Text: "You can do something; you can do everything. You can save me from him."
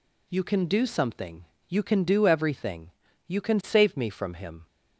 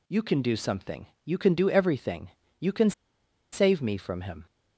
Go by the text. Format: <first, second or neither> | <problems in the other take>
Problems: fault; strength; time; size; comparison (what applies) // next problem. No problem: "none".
first | pauses between "can" and "save"; noticeable; at 2.9 s; 0.61 s long